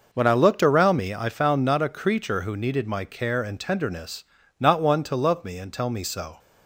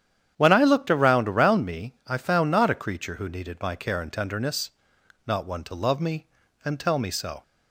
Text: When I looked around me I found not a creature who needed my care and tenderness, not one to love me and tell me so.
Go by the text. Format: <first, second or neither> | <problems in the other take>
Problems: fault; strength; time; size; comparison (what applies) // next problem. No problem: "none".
first | starts louder than the rest; strong; until 1.3 s; 9.5 dB // says "around" twice; at 1.2 s